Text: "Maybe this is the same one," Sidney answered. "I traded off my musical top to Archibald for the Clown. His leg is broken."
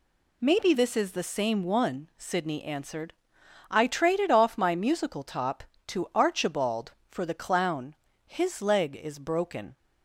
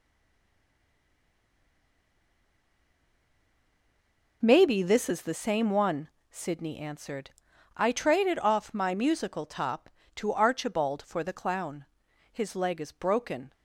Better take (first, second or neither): first